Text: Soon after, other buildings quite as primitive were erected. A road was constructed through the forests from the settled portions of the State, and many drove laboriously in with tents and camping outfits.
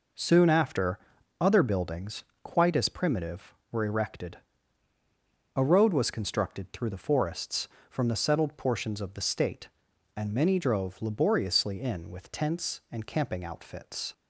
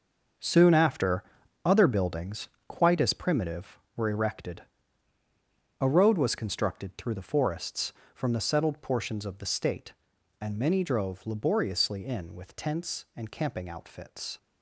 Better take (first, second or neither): first